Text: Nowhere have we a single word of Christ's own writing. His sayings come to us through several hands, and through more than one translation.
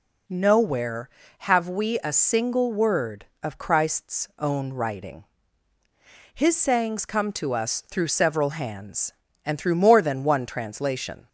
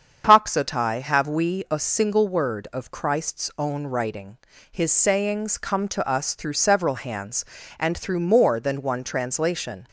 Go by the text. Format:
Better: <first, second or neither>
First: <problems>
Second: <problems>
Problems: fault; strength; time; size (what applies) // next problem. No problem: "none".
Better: first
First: none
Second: starts louder than the rest; strong; until 1.2 s; 7.5 dB // says "Toxotai" for "Nowhere"; at 0.2 s